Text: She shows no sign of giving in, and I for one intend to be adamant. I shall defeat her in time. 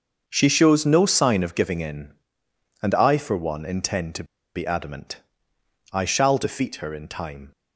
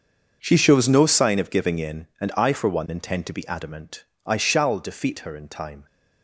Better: second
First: starts louder than the rest; until 1.2 s; 6.5 dB // pauses between "to" and "be"; slight; at 4.2 s; 0.31 s long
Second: starts louder than the rest; until 1.4 s; 6.5 dB

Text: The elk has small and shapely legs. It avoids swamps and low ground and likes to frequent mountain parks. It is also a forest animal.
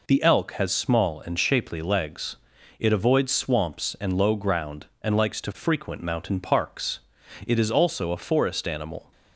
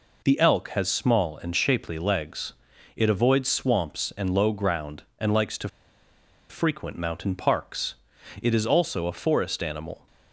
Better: first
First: none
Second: pauses between "to" and "frequent"; noticeable; at 5.6 s; 0.81 s long

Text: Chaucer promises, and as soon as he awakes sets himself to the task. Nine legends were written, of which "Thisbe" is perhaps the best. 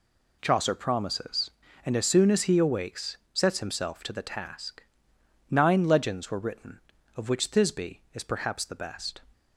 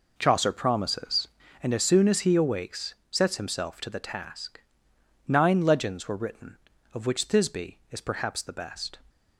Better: first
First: pauses between "awakes" and "sets"; slight; at 3.1 s; 0.16 s long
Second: starts louder than the rest; noticeable; until 1.7 s; 4.5 dB // pauses between "awakes" and "sets"; slight; at 2.9 s; 0.16 s long

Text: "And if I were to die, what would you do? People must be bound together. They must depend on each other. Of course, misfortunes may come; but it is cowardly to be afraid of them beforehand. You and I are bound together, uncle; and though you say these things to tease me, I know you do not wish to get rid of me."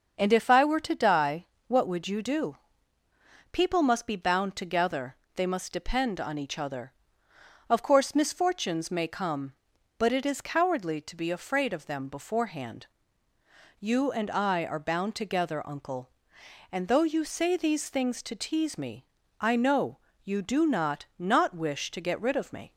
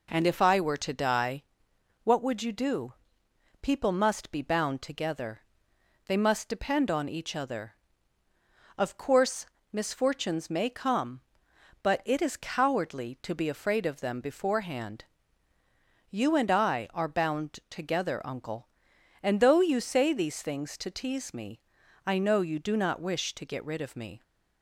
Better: second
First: starts louder than the rest; until 1.1 s; 6.5 dB // pauses between "know" and "you"; slight; at 19.9 s; 0.28 s long // says "not" twice; at 21.1 s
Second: none

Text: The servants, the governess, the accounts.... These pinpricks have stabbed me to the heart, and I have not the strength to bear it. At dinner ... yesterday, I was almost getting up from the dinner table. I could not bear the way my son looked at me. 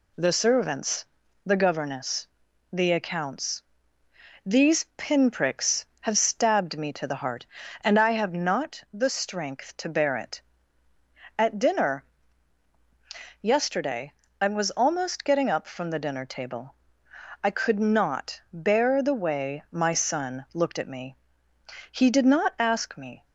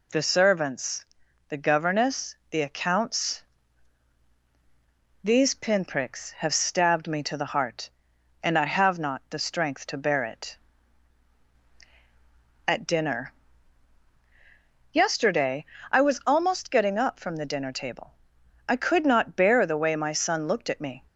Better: second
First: goes on to say "He did not ask me"; from 21.8 s on; 1.3 s long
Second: none

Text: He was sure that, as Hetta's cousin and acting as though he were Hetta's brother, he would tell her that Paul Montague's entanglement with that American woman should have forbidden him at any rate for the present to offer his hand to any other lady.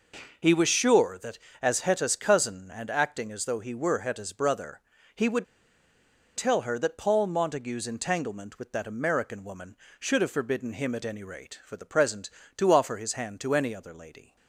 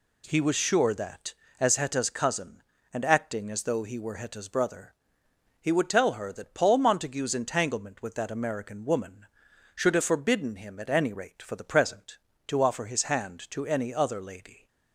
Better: second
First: pauses between "would" and "tell"; noticeable; at 5.4 s; 0.91 s long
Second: none

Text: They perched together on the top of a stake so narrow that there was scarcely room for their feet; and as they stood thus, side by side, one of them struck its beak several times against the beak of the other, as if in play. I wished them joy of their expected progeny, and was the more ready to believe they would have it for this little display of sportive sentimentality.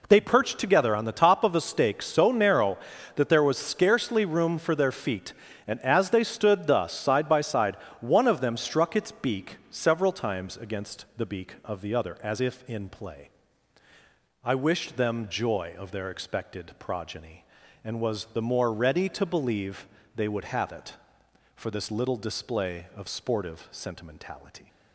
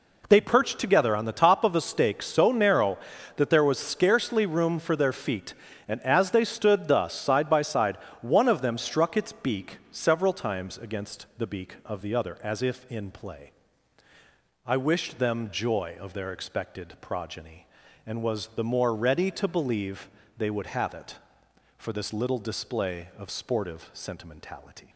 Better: neither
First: pauses between "believe" and "they"; slight; at 19.8 s; 0.30 s long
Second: pauses between "believe" and "they"; slight; at 20.0 s; 0.30 s long

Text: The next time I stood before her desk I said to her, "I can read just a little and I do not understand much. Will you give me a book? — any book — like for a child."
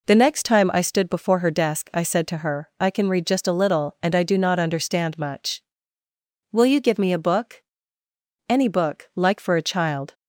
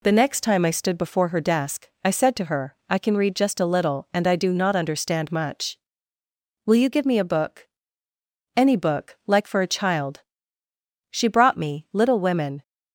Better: first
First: none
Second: pauses between "desk" and "I"; slight; at 1.8 s; 0.16 s long // goes on to say "She brought me Little Women"; from 11.1 s on; 1.5 s long

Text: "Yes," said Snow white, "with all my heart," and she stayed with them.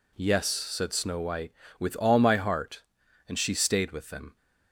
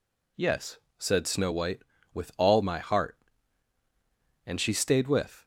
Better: first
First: none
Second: stops before "them"; at 5.4 s

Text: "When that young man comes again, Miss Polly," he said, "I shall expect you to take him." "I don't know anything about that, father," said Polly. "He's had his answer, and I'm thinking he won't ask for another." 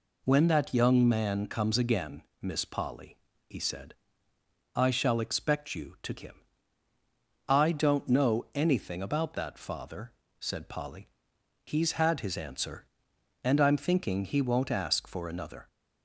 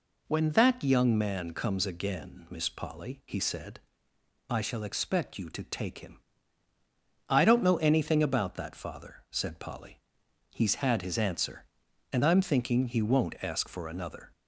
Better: second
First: skips "take"; at 6.1 s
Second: none

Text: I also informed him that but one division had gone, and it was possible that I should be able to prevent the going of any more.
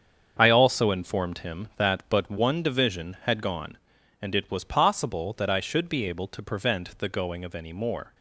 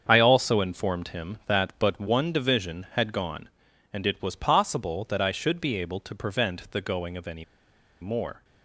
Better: first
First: starts louder than the rest; strong; until 1.4 s; 7 dB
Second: starts louder than the rest; strong; until 1.1 s; 7 dB // pauses between "any" and "more"; noticeable; at 7.4 s; 0.57 s long

